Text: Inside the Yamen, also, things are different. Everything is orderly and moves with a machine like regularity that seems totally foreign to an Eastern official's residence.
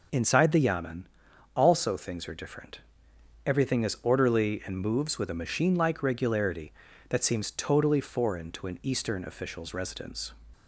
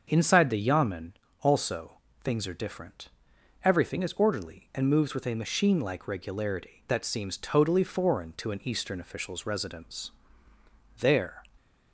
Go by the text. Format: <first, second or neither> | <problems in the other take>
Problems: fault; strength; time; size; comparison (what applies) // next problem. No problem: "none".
first | starts louder than the rest; until 1.1 s; 6.5 dB // goes on to say "There"; slight; from 11.0 s on; 0.42 s long